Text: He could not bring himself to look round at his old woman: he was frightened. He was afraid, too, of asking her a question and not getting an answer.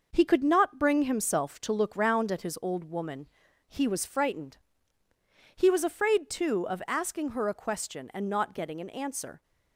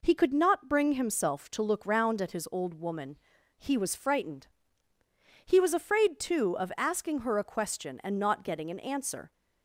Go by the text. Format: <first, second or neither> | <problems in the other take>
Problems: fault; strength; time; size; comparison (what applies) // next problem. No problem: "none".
second | gets quieter; noticeable; throughout; 6 dB